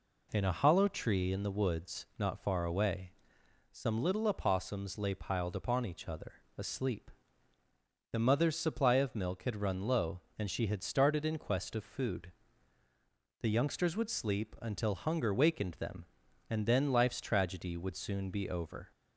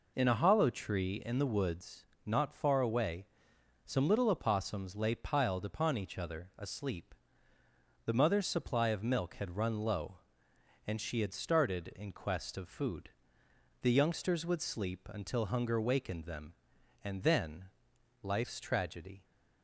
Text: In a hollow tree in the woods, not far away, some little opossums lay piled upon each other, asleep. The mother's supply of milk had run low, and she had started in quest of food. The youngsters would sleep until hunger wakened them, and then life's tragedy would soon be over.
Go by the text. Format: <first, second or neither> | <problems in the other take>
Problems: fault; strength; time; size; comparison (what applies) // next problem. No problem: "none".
first | pauses between "then" and "life's"; noticeable; at 17.6 s; 0.58 s long // stops before "would soon be over"; at 19.2 s